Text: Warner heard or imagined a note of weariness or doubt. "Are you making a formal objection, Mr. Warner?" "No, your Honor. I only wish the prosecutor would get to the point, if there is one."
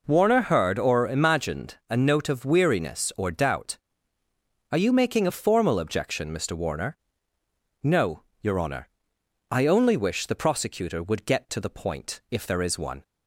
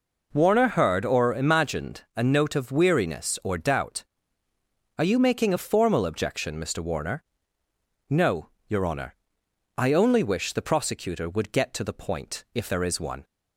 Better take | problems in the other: neither | none

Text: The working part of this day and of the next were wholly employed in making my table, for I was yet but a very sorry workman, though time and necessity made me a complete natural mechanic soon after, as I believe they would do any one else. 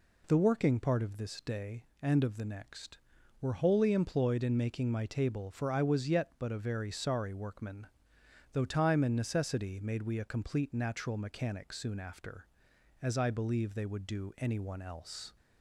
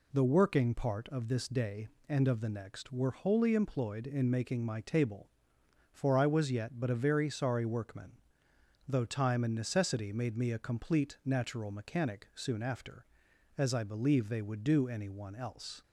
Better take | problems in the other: second | says "we" for "me"; at 10.0 s

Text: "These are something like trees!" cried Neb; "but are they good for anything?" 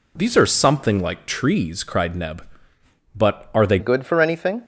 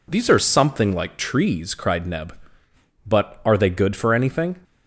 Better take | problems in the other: second | changes voice at "good"; from 3.7 s on; 0.9 s long

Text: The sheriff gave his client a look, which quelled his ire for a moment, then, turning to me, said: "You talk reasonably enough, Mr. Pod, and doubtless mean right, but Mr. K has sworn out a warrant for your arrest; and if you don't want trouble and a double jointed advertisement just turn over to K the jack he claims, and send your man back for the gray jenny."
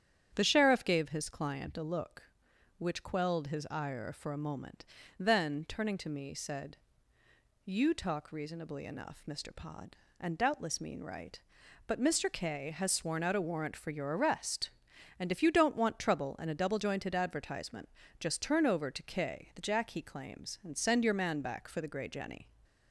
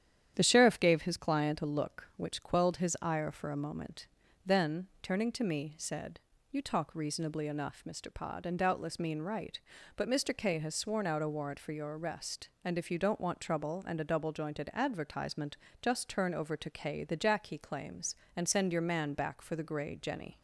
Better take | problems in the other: neither | starts louder than the rest; strong; the same in both // pauses between "advertisement" and "just"; slight; the same in both

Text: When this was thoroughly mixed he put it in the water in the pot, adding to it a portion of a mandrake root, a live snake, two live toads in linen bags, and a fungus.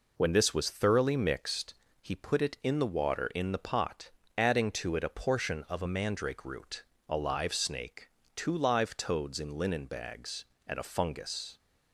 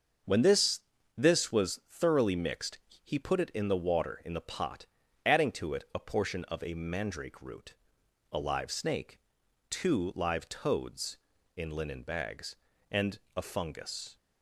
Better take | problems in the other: first | starts louder than the rest; until 1.6 s; 7 dB // says "this" twice; at 1.1 s // pauses between "mixed" and "he"; slight; at 2.7 s; 0.26 s long; slight in the first // pauses between "and" and "a"; slight; at 13.1 s; 0.16 s long

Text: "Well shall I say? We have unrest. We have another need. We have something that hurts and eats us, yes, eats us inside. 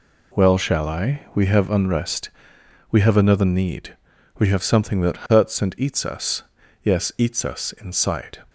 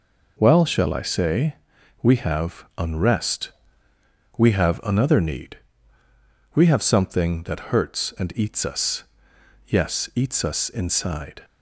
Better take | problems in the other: second | skips "say"; at 1.2 s

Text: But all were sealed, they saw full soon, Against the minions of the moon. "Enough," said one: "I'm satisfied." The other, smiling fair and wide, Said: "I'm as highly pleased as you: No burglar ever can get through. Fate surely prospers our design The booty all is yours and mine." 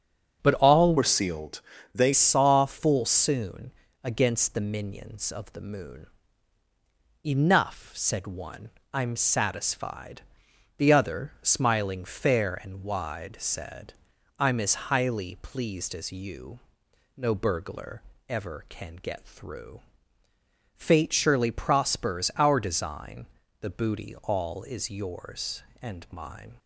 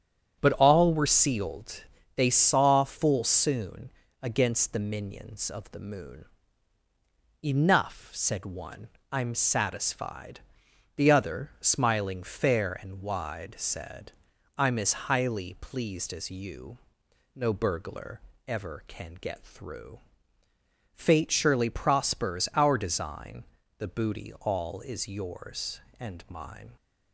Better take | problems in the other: second | starts louder than the rest; strong; until 1.4 s; 7 dB; strong in the second // changes voice from "were" to "they"; from 0.9 to 2.1 s; 1.2 s long // pauses between "burglar" and "ever"; slight; at 18.0 s; 0.28 s long; slight in the second // pauses between "design" and "The"; slight; at 23.2 s; 0.34 s long; slight in the second

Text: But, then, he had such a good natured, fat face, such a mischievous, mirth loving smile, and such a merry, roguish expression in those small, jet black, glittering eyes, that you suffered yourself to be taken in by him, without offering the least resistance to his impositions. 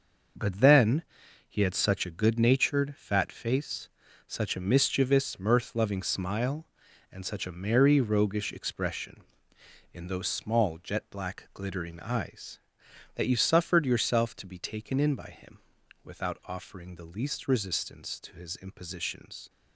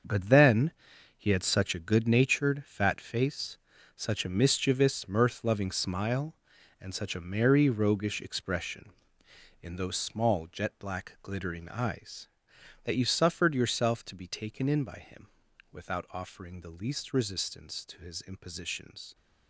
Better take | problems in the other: first | gets quieter; strong; throughout; 10.5 dB

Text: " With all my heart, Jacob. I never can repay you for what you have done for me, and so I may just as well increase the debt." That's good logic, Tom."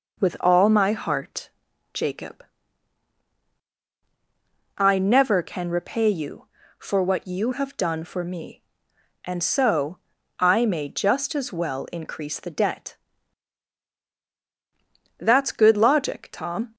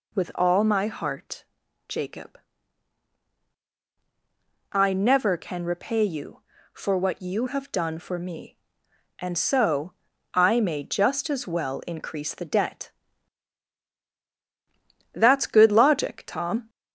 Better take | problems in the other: first | gets louder; slight; throughout; 2.5 dB // pauses between "so" and "I"; at 9.9 s; 0.42 s long; also in the first

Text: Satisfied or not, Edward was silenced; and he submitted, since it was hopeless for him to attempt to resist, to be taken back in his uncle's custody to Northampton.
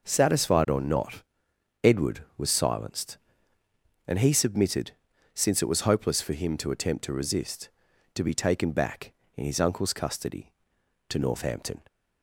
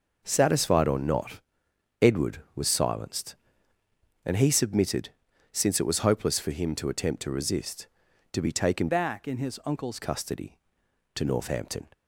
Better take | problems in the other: first | changes voice from "back" to "uncle's"; from 8.8 to 9.9 s; 1.1 s long

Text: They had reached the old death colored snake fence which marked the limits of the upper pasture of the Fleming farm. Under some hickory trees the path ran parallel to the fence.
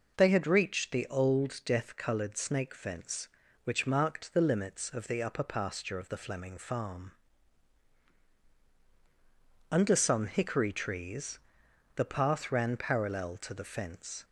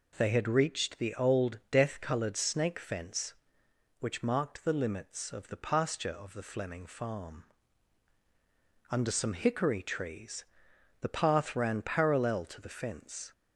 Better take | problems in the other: first | skips "upper"; at 5.5 s // pauses between "trees" and "the"; noticeable; at 10.4 s; 0.56 s long; noticeable in the first

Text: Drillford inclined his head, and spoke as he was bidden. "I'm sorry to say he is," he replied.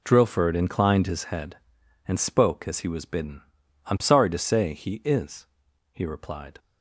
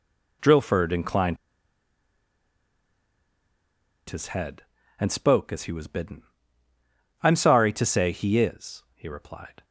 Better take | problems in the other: first | pauses between "inclined" and "his"; strong; at 1.3 s; 2.7 s long

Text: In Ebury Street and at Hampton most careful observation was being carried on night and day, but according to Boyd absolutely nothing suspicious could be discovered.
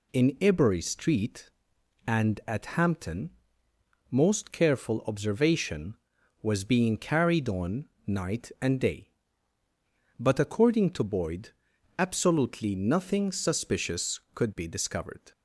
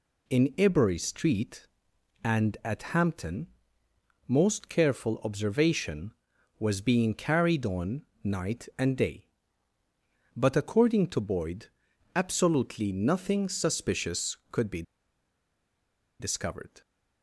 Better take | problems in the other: first | pauses between "Hampton" and "most"; noticeable; at 3.4 s; 0.80 s long; noticeable in the first // pauses between "on" and "night"; slight; at 8.0 s; 0.22 s long; slight in the first // pauses between "Boyd" and "absolutely"; noticeable; at 11.6 s; 0.48 s long; noticeable in the first // pauses between "be" and "discovered"; strong; at 14.8 s; 1.3 s long

